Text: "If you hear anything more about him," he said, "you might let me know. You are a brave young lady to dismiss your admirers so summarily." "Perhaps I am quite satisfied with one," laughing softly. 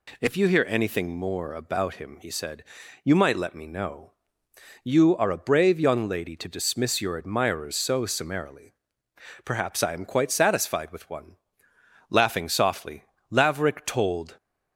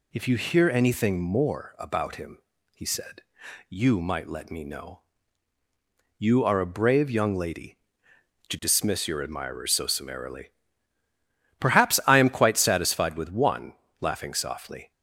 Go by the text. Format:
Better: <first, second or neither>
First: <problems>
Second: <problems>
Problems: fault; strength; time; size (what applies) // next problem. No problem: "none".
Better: second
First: goes on to say "Laverick told"; noticeable; from 13.3 s on; 1.0 s long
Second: none